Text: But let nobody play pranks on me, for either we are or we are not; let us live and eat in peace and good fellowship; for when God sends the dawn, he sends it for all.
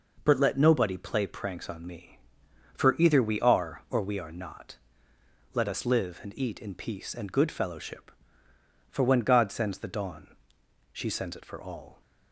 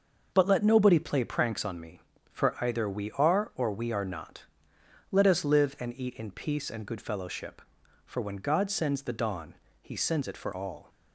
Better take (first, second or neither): second